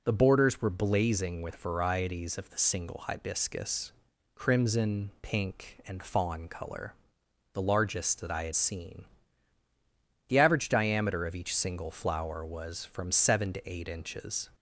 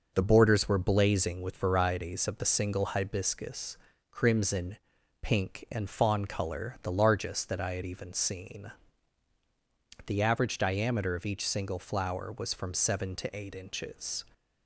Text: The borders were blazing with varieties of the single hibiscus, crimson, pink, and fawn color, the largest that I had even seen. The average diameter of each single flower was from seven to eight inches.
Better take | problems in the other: second | skips "even"; at 8.5 s

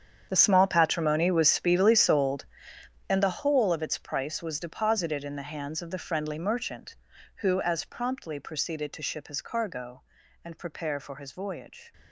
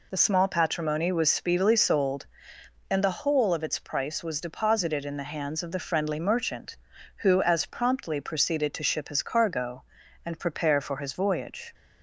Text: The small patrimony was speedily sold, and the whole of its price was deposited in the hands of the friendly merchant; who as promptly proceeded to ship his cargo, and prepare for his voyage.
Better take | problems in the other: second | gets quieter; strong; throughout; 16.5 dB

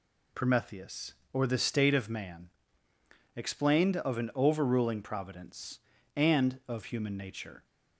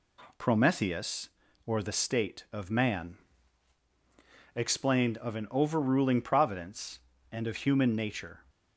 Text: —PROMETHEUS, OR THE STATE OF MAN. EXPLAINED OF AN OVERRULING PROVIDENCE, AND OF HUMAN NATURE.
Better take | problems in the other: neither | none

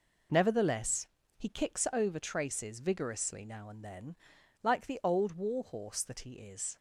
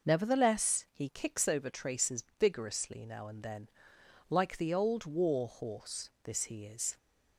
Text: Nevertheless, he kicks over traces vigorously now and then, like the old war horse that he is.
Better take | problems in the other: first | pauses between "traces" and "vigorously"; slight; at 2.2 s; 0.16 s long // says "this" for "that"; at 6.2 s

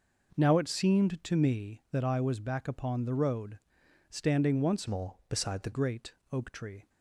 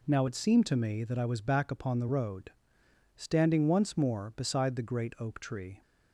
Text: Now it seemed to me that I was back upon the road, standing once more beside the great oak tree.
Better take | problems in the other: second | changes voice from "more" to "the"; from 4.8 to 5.7 s; 0.9 s long // pauses between "great" and "oak"; slight; at 6.1 s; 0.18 s long

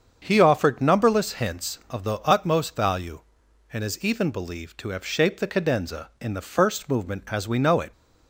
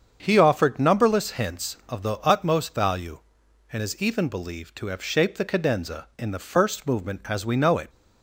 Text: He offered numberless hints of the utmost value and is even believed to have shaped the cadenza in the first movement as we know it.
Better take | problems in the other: neither | starts louder than the rest; strong; the same in both

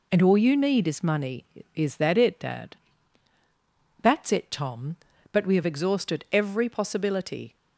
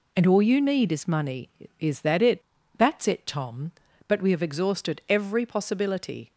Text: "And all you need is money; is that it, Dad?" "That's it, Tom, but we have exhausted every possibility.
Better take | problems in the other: first | skips "Dad"; at 2.6 s

